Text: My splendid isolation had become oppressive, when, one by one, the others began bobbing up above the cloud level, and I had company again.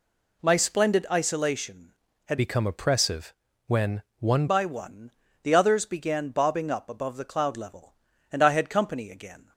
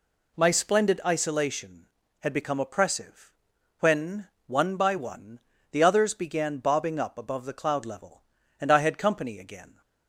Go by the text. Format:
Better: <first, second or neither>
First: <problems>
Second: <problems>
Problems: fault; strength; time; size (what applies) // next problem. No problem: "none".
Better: second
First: changes voice from "become" to "one"; from 2.3 to 4.4 s; 2.1 s long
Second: none